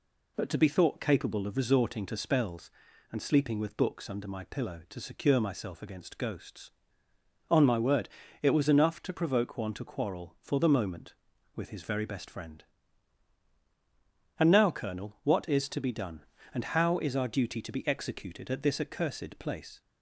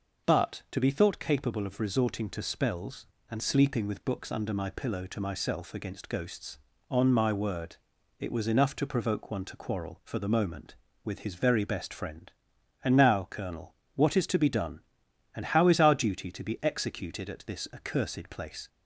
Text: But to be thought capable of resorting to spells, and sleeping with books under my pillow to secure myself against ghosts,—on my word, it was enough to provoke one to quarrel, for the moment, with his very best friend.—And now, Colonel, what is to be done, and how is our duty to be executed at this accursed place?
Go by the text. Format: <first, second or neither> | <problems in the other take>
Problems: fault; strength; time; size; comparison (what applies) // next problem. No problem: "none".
first | skips "secure"; at 5.2 s